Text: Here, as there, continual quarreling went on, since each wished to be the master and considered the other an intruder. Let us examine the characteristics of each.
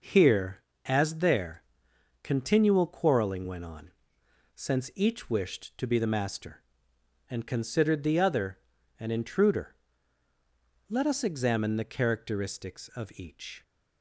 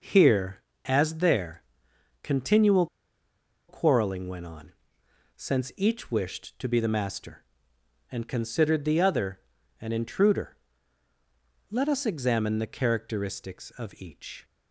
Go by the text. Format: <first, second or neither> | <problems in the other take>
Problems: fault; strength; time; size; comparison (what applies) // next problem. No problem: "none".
first | pauses between "continual" and "quarreling"; noticeable; at 2.8 s; 0.84 s long // pauses between "other" and "an"; at 9.3 s; 0.42 s long; also in the first